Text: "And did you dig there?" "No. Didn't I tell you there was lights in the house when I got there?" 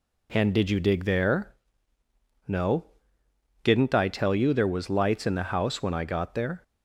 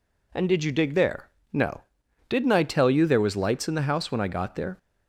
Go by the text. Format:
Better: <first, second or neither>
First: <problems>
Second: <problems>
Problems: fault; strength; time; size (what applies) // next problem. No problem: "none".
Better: neither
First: none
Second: none